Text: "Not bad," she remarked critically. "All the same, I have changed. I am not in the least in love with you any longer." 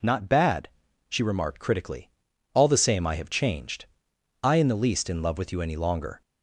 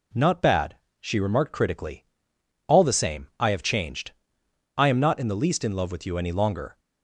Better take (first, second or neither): second